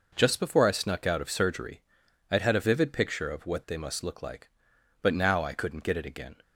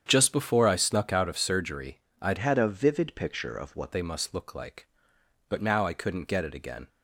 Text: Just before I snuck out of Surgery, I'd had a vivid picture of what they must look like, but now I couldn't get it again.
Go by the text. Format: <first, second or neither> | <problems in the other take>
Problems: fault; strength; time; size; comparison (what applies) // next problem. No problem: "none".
first | starts louder than the rest; strong; until 1.0 s; 8.5 dB // changes voice from "had" to "what"; from 2.3 to 3.9 s; 1.6 s long